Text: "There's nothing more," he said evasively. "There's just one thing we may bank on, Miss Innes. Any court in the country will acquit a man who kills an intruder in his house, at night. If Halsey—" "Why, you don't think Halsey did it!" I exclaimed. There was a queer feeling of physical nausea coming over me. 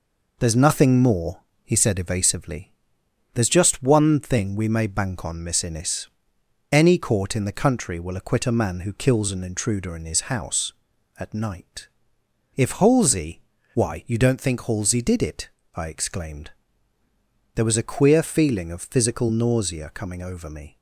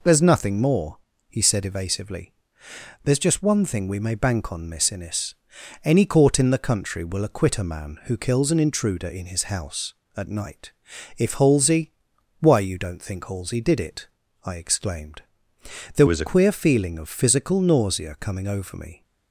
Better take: first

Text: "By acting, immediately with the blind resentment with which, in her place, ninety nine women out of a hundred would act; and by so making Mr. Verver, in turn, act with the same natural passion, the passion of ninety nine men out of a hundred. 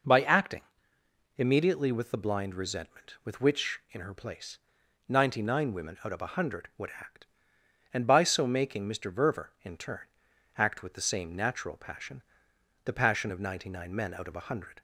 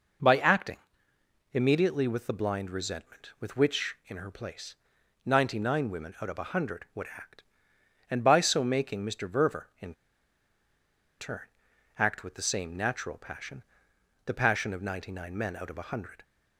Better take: first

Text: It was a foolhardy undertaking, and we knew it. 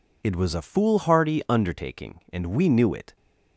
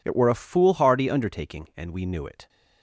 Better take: first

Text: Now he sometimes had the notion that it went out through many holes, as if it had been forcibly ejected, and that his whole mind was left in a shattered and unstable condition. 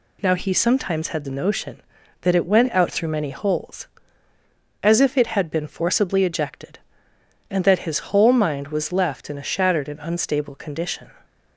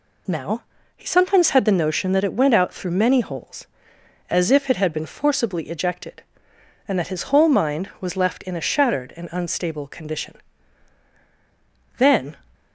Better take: first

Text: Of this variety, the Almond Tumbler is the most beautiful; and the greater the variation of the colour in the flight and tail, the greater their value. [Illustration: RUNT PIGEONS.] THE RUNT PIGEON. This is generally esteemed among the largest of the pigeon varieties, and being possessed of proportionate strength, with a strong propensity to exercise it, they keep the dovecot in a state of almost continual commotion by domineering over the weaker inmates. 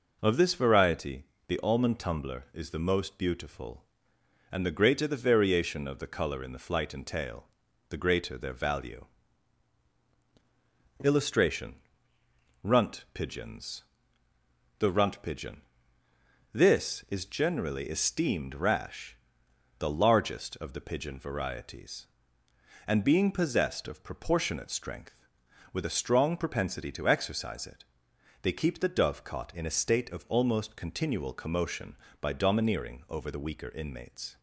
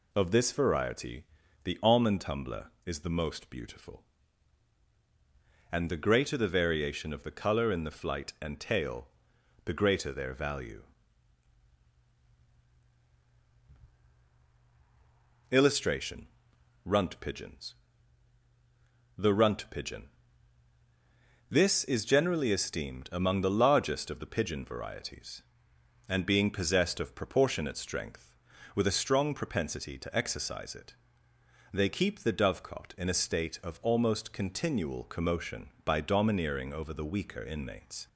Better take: second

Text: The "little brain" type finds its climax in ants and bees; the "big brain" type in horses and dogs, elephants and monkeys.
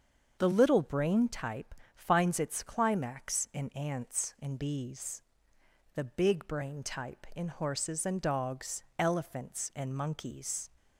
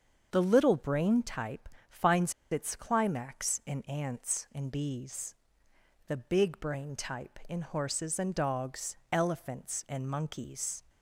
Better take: first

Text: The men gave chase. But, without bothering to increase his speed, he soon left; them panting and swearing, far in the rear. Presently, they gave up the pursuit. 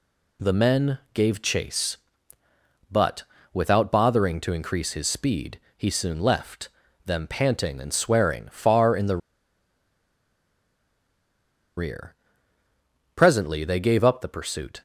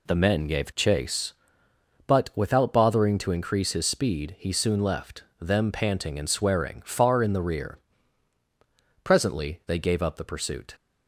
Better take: second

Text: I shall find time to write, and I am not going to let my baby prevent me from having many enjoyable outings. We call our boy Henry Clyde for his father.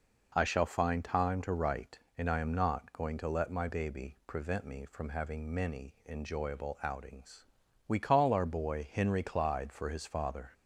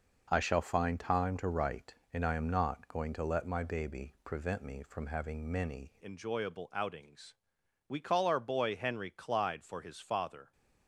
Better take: first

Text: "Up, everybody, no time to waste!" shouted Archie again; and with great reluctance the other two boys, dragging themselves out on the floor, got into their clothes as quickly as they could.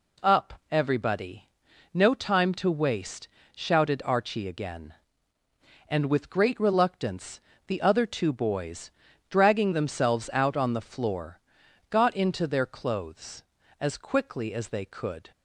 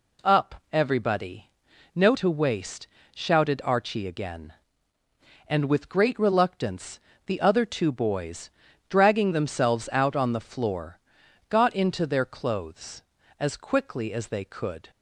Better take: first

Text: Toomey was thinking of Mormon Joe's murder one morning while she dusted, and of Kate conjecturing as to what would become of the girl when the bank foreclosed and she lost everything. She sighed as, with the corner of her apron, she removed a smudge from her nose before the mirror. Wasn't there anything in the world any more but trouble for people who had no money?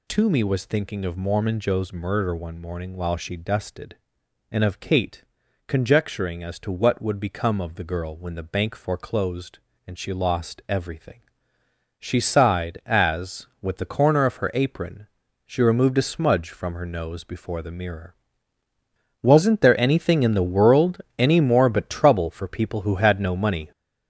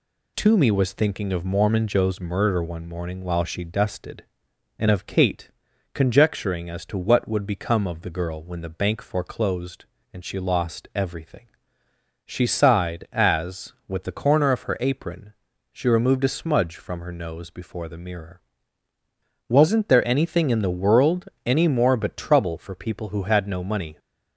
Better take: second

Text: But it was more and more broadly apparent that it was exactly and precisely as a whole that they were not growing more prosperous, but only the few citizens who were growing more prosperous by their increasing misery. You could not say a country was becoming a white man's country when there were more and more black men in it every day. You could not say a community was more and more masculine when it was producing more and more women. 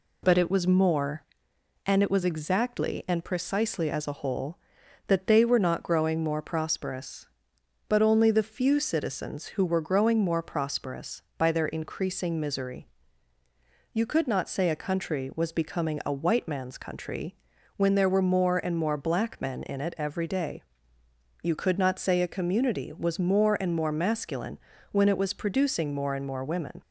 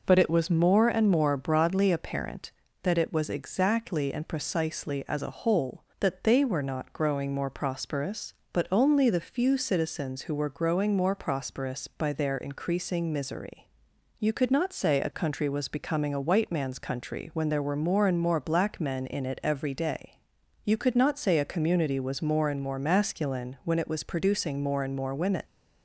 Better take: second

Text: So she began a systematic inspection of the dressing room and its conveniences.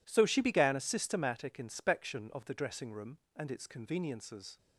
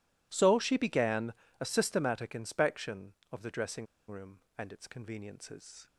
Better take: first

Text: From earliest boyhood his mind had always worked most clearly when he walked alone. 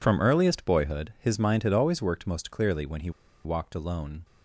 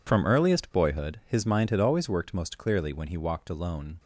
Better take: second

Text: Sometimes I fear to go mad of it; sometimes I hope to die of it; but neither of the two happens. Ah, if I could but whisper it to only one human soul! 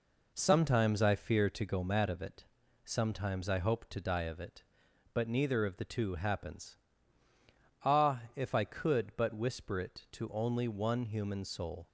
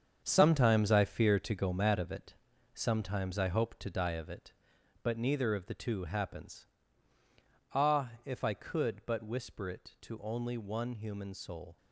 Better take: first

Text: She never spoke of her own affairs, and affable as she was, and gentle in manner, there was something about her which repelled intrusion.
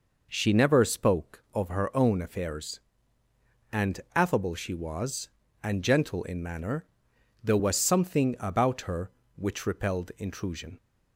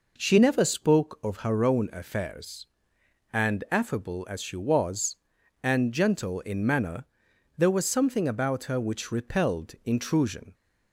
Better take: second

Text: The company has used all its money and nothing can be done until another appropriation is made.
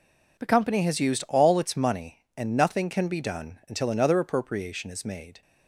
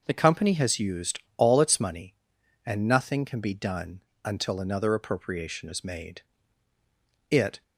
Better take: first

